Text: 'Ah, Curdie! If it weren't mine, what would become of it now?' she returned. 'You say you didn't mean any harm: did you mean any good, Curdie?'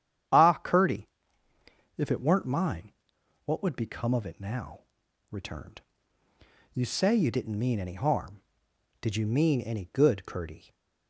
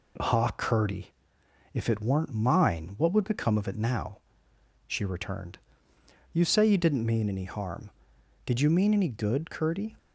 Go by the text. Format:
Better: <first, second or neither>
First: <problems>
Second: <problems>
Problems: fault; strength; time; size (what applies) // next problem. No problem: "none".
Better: second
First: starts louder than the rest; strong; until 2.2 s; 9.5 dB // skips "she"; at 5.0 s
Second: none